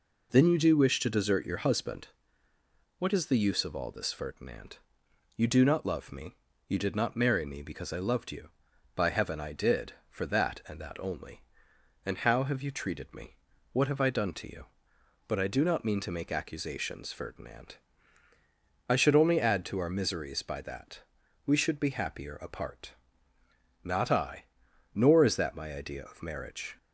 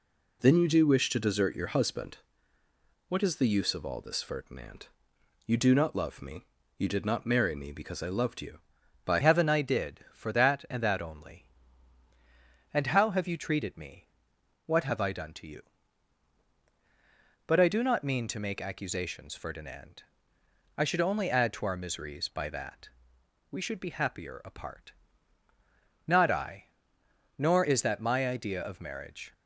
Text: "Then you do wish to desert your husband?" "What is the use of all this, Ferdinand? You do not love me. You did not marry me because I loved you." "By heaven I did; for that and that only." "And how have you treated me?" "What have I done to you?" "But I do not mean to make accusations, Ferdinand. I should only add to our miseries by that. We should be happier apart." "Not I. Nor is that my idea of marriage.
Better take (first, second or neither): first